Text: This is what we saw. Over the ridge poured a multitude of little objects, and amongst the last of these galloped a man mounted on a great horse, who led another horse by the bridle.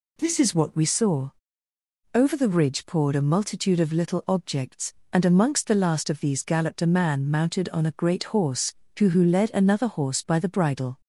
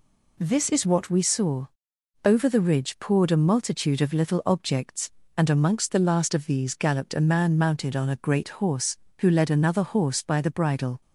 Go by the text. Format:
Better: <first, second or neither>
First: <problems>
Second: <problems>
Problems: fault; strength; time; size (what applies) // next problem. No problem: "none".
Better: second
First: says "who" twice; at 9.0 s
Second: none